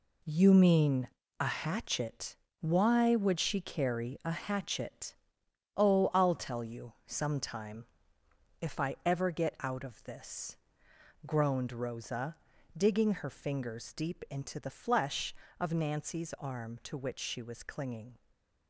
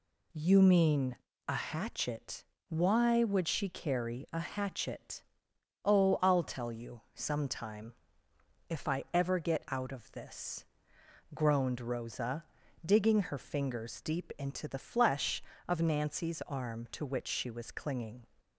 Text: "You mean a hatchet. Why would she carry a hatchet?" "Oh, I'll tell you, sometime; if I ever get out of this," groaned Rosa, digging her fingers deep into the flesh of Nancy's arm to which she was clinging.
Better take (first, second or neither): second